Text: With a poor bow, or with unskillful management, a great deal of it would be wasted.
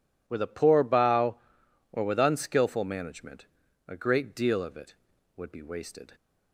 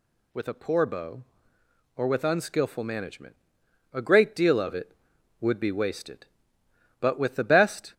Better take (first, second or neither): first